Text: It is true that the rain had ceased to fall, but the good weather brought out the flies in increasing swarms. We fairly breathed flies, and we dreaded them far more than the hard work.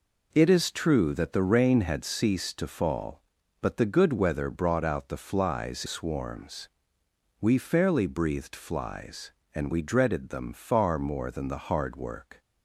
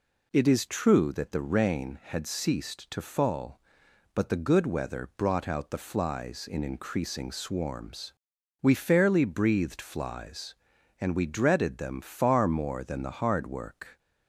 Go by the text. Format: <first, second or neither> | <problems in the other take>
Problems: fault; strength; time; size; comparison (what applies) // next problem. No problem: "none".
second | skips "in increasing"; at 5.8 s